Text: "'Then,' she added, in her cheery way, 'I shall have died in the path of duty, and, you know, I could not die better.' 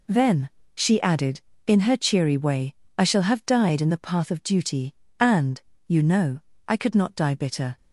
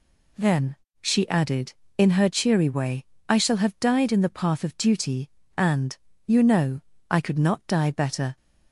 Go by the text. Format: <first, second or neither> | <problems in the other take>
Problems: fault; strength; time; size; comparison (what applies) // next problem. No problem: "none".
second | says "bitter" for "better"; at 7.3 s